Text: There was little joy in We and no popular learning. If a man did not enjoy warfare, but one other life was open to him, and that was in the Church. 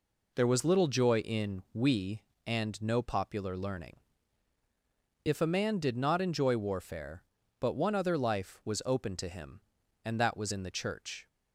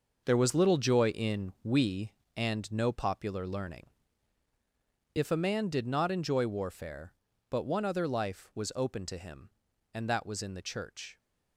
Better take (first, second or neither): first